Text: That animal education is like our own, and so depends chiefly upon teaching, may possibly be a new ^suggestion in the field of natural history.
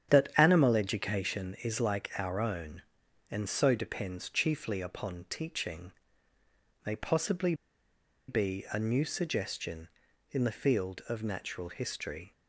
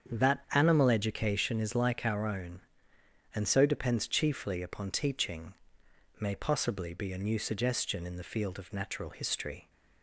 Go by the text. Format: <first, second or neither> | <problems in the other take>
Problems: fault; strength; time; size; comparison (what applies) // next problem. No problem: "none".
second | starts louder than the rest; strong; until 1.1 s; 9 dB; strong in the second // pauses between "possibly" and "be"; noticeable; at 7.5 s; 0.74 s long